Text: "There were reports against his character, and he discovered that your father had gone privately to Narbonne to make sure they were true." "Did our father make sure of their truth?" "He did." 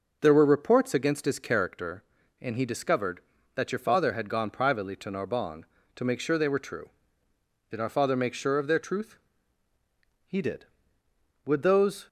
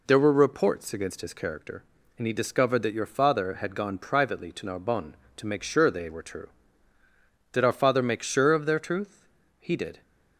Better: second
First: goes on to say "Would those"; noticeable; from 11.4 s on; 0.62 s long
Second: none

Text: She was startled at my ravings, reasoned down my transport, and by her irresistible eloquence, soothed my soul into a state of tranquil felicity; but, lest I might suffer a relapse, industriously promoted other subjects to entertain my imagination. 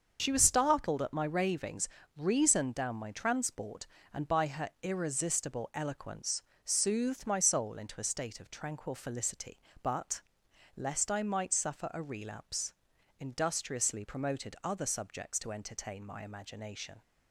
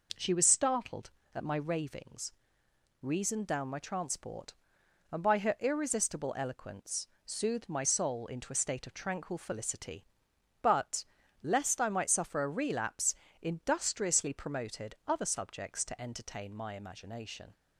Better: second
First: loses the start of "She"; at 0.1 s; 40 ms // starts louder than the rest; until 1.2 s; 6.5 dB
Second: none

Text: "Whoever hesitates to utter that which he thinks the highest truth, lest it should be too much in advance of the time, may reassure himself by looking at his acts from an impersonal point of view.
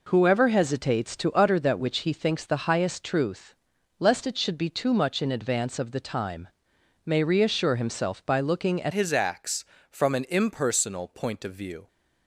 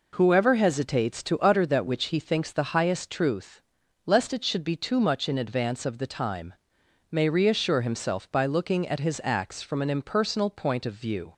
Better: second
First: changes voice at "his"; from 8.9 s on; 2.9 s long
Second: none

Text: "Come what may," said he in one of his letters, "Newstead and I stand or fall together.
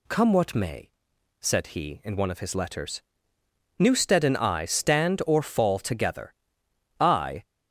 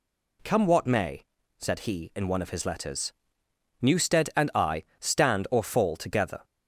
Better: second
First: goes on to say "I"; slight; from 6.9 s on; 0.44 s long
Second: none

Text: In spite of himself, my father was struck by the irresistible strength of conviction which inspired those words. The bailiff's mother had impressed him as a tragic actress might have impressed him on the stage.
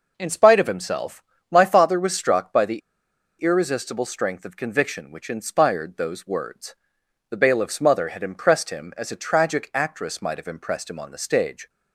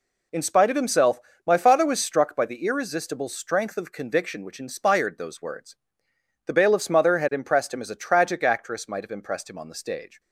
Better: second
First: pauses between "the" and "irresistible"; noticeable; at 2.7 s; 0.60 s long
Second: none

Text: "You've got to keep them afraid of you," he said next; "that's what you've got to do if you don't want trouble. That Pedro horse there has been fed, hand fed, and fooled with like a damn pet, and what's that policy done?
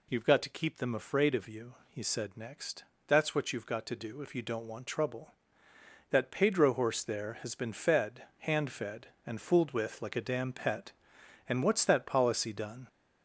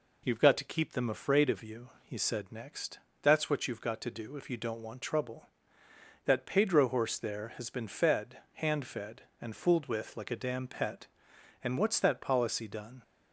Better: second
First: gets louder; noticeable; throughout; 4.5 dB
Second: none

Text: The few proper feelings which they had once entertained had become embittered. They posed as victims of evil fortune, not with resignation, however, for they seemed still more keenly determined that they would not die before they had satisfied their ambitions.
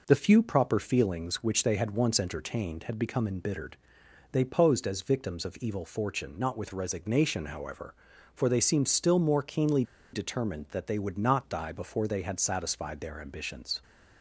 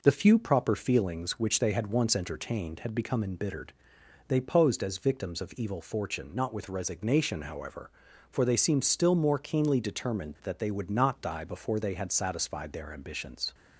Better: second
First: pauses between "keenly" and "determined"; slight; at 9.8 s; 0.28 s long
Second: none

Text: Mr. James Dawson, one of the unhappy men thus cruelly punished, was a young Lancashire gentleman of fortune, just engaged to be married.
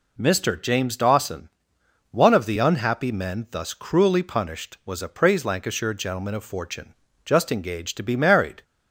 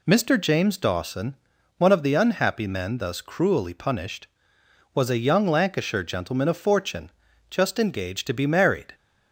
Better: second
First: says "praise" for "young"; at 5.0 s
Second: none

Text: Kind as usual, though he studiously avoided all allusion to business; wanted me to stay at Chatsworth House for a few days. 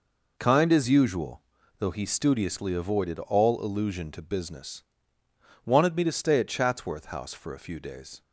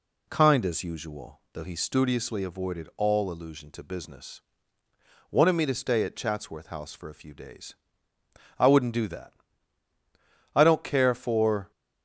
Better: first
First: none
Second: goes on to say "I wouldn't do that I don't care for"; strong; from 8.5 s on; 3.1 s long

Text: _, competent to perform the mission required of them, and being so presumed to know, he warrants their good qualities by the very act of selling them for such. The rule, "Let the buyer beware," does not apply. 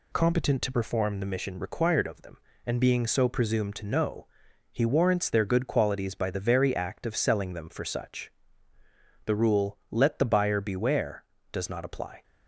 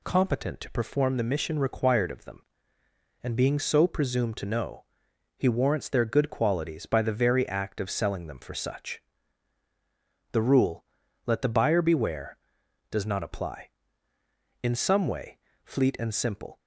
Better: first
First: none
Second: goes on to say "In some way Fleet and Simple"; strong; from 14.6 s on; 1.9 s long

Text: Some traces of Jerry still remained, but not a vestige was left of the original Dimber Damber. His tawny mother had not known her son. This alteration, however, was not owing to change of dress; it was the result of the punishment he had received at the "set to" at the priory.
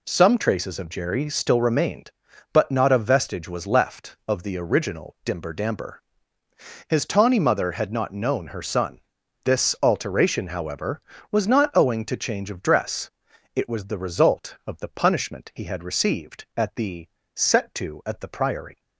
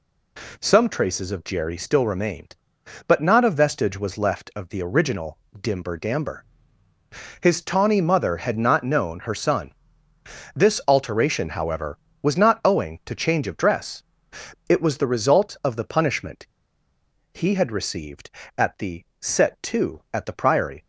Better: first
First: pauses between "the" and "set"; slight; at 17.0 s; 0.26 s long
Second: pauses between "original" and "Dimber"; slight; at 5.3 s; 0.20 s long // pauses between "punishment" and "he"; noticeable; at 16.4 s; 0.86 s long // pauses between "the" and "set"; slight; at 19.0 s; 0.18 s long

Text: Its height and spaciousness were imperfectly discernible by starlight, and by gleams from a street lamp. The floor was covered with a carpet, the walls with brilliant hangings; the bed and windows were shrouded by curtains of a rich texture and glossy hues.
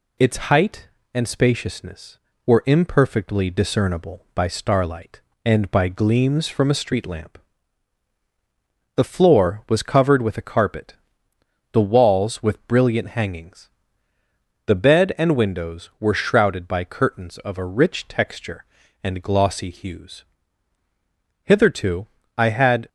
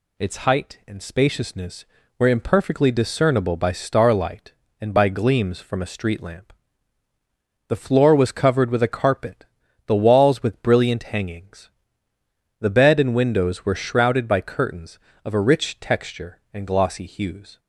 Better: second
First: goes on to say "Hitherto I had"; from 21.4 s on; 1.4 s long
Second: none

